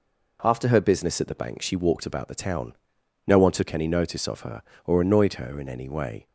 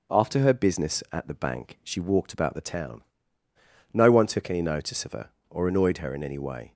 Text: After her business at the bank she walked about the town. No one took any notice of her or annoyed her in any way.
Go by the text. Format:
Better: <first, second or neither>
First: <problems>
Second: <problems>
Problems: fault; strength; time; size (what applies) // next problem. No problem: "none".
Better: neither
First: none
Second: none